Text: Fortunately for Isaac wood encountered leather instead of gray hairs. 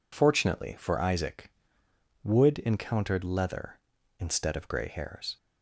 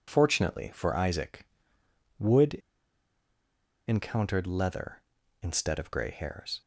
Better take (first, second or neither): first